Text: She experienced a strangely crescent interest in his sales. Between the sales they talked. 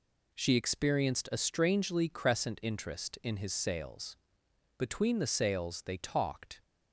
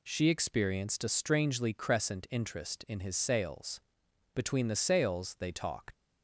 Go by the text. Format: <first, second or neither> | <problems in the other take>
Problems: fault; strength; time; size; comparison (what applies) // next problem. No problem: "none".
first | leaves "talked" unfinished; at 5.9 s; 110 ms